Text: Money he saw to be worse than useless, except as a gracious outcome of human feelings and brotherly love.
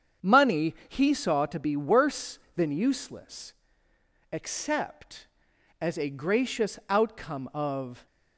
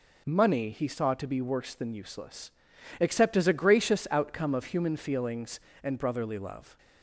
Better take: second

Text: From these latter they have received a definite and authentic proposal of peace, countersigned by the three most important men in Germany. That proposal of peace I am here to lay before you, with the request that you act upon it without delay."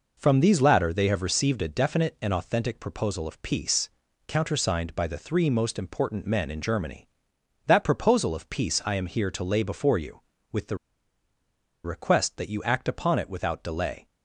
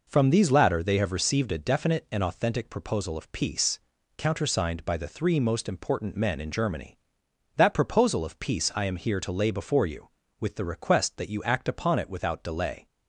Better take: second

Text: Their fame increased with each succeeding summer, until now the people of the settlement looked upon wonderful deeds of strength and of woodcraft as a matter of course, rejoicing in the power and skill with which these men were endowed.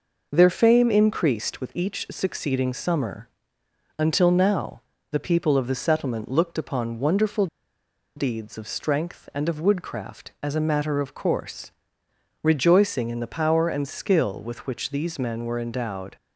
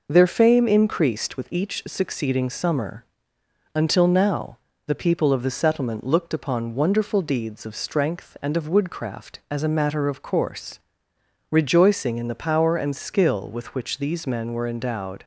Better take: second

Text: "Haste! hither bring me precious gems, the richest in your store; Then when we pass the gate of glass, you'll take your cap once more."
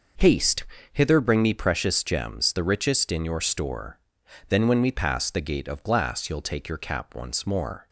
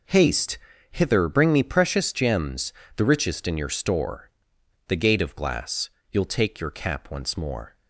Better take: first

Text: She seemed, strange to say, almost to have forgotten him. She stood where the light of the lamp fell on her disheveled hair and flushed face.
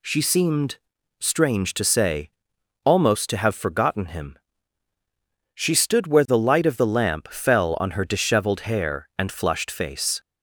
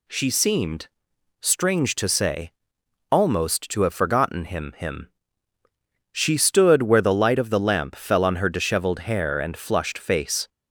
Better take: first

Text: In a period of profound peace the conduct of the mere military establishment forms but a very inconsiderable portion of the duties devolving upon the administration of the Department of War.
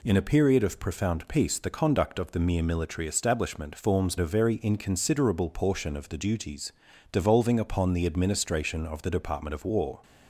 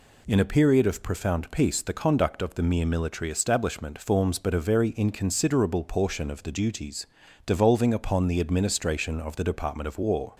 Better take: second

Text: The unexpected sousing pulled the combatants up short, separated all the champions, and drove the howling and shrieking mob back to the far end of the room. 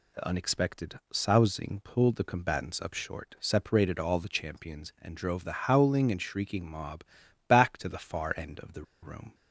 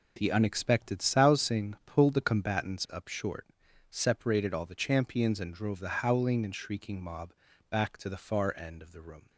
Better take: second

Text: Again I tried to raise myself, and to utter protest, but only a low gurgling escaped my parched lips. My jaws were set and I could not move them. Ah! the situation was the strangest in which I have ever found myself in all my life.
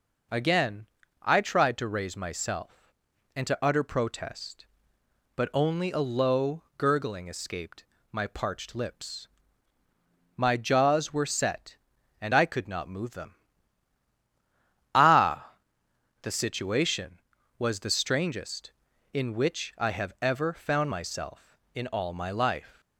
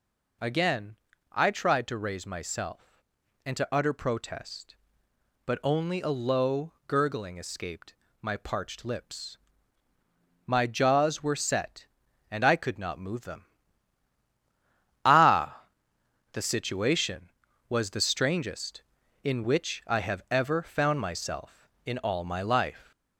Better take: first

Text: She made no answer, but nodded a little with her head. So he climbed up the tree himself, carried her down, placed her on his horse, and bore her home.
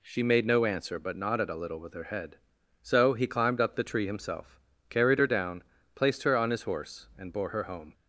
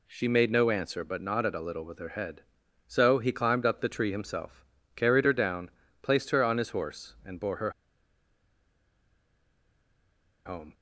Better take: first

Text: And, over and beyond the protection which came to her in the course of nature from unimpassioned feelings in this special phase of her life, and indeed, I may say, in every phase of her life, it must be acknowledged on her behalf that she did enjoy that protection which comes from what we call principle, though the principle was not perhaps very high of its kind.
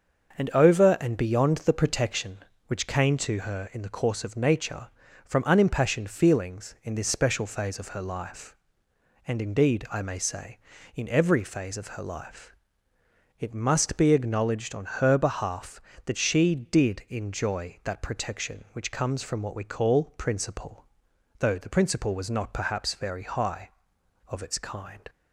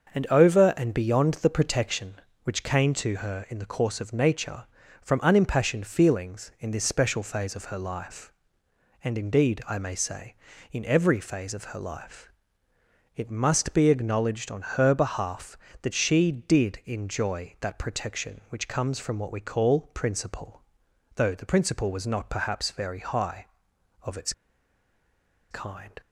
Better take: first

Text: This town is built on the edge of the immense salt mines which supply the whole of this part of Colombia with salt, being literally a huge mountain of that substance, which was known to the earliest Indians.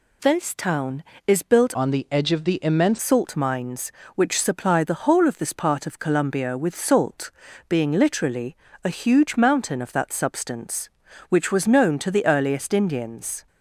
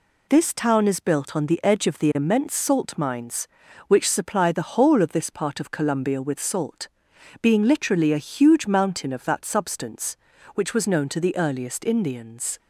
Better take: second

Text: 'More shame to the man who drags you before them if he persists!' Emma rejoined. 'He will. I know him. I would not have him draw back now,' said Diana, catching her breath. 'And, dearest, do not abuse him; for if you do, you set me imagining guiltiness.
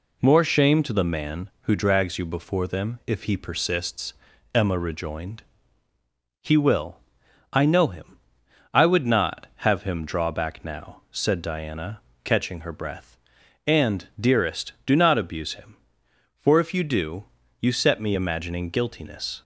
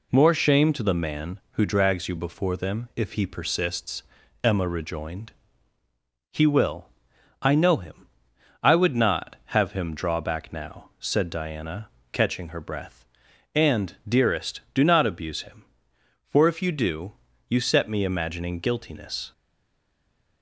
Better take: first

